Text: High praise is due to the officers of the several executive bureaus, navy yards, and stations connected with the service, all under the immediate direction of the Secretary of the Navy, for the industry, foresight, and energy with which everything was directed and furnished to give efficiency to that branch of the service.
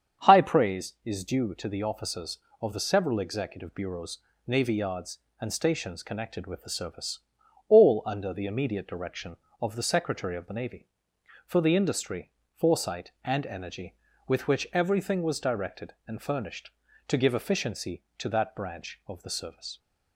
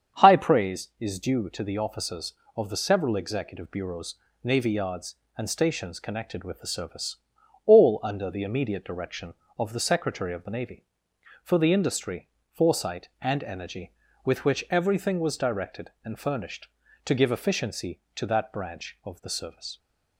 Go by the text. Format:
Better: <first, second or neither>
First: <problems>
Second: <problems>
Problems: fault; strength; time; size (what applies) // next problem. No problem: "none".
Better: neither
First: starts louder than the rest; strong; until 1.3 s; 7.5 dB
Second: starts louder than the rest; strong; until 1.2 s; 7.5 dB